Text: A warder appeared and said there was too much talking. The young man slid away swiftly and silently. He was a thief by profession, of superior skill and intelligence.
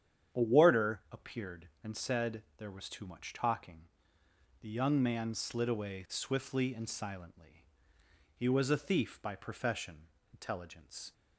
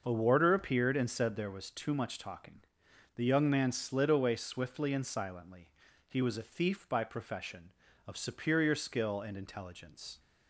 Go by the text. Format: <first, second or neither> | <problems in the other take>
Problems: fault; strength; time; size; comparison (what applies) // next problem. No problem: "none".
second | starts louder than the rest; strong; until 1.4 s; 9 dB; also in the second // skips "of superior skill and"; at 10.1 s